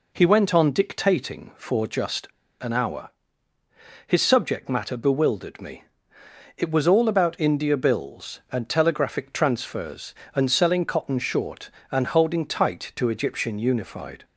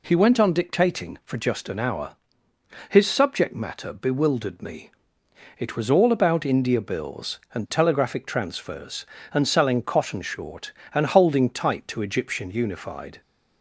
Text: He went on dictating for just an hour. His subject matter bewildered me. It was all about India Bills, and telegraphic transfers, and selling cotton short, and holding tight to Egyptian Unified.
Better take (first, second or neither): second